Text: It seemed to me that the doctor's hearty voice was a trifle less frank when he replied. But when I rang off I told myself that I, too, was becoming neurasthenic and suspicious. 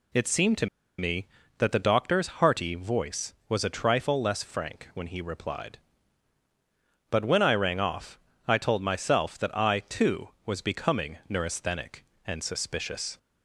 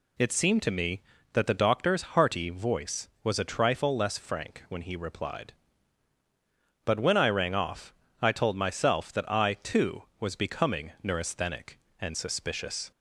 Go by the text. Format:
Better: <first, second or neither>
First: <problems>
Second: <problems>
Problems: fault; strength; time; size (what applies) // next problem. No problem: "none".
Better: second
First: pauses between "to" and "me"; slight; at 0.6 s; 0.32 s long // pauses between "off" and "I"; slight; at 8.1 s; 0.30 s long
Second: pauses between "off" and "I"; slight; at 7.9 s; 0.29 s long